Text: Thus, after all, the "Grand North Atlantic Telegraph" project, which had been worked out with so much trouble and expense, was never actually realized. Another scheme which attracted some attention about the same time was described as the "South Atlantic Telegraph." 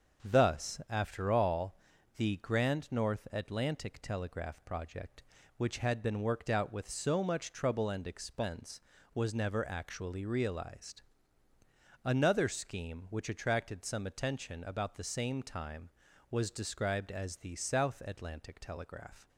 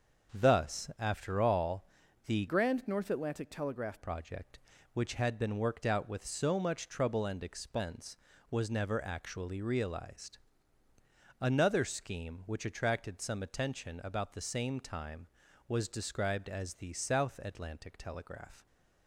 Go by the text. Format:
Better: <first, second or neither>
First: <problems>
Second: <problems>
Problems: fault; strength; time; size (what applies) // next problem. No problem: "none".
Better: first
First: starts louder than the rest; until 1.3 s; 6.5 dB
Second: starts louder than the rest; until 1.4 s; 6.5 dB // changes voice from "Grand" to "Telegraph"; from 2.4 to 4.0 s; 1.6 s long